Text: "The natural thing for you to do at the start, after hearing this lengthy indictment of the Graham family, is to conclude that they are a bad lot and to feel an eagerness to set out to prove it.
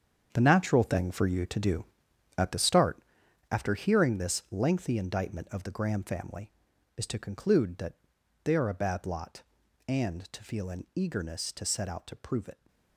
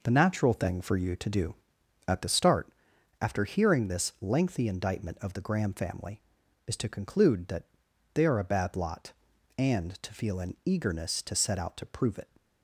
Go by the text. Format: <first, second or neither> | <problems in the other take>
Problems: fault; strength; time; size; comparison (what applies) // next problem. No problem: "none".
second | gets quieter; strong; throughout; 11 dB // pauses between "that" and "they"; noticeable; at 7.9 s; 0.48 s long; noticeable in the second